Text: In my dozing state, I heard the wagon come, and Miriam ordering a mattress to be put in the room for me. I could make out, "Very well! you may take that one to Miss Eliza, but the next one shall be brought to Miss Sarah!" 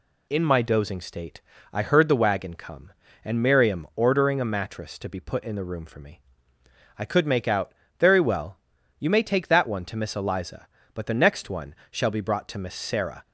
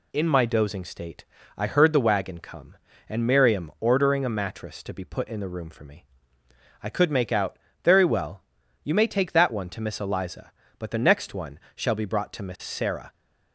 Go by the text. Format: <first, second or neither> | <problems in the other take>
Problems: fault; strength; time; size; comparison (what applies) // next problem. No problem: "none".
neither | pauses between "one" and "shall"; slight; the same in both